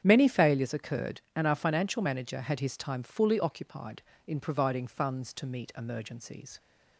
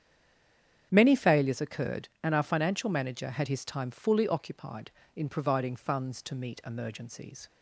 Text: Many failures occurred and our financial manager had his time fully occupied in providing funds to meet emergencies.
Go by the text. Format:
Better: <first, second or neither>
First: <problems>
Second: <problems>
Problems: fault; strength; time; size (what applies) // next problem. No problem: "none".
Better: first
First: starts louder than the rest; strong; until 1.0 s; 8 dB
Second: stays silent before the first word; slight; until 0.9 s; 0.9 s long // starts louder than the rest; strong; until 1.9 s; 8 dB